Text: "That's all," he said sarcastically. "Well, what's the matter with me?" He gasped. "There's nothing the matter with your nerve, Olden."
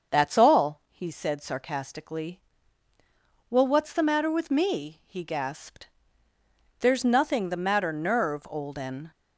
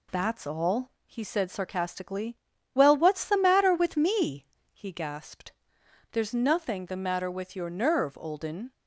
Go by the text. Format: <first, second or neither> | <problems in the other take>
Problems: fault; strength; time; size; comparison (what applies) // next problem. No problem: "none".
second | starts louder than the rest; until 1.1 s; 6.5 dB // skips "with your"; at 7.9 s